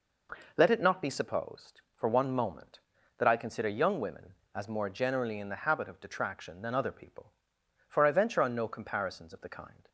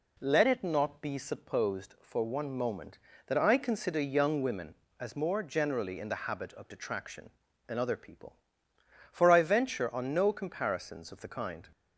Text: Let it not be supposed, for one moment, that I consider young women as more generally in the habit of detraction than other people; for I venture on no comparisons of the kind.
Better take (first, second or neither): neither